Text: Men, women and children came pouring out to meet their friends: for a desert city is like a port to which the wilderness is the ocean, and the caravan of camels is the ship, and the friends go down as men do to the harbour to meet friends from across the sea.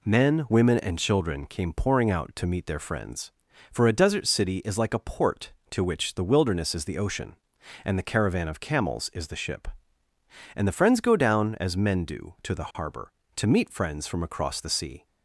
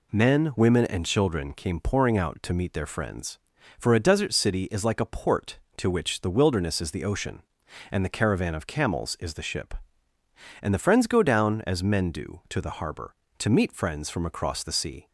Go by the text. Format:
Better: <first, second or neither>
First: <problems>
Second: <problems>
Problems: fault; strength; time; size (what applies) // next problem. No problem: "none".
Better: neither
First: none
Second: none